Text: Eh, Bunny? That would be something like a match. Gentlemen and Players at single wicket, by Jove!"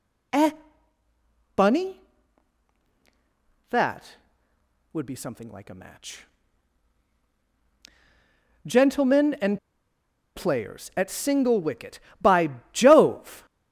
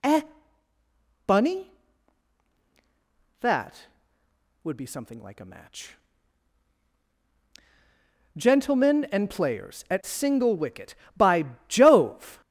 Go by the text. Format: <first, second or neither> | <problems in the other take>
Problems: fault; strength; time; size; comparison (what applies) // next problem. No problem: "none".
second | pauses between "and" and "Players"; noticeable; at 9.5 s; 0.77 s long // pauses between "by" and "Jove"; slight; at 12.4 s; 0.24 s long; slight in the second